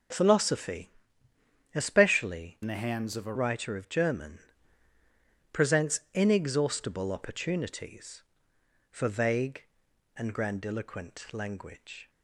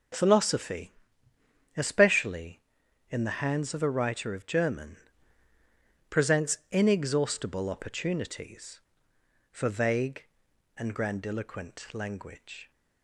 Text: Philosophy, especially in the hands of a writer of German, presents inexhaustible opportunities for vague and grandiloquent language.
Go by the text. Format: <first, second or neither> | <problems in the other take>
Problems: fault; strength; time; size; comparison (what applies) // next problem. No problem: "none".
second | changes voice from "in" to "a"; from 2.6 to 3.3 s; 0.7 s long